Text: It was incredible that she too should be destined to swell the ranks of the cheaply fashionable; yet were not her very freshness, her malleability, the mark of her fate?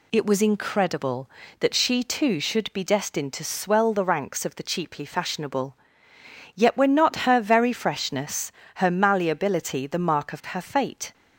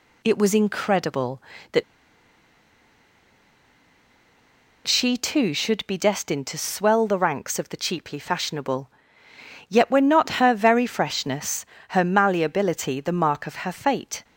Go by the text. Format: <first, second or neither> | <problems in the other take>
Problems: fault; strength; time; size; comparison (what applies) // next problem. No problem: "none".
first | pauses between "that" and "she"; strong; at 1.8 s; 3.0 s long